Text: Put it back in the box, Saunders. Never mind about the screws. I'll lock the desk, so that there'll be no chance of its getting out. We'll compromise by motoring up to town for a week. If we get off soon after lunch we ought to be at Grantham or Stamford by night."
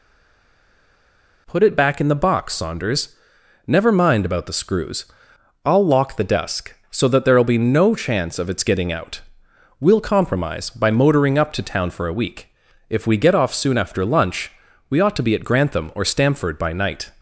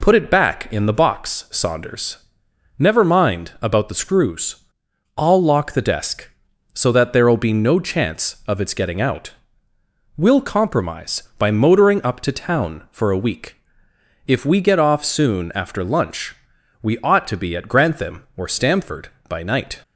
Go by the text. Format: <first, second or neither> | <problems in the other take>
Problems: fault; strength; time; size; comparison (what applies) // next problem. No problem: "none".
second | stays silent before the first word; noticeable; until 1.4 s; 1.4 s long // pauses between "lunch" and "we"; at 14.5 s; 0.38 s long; noticeable in the second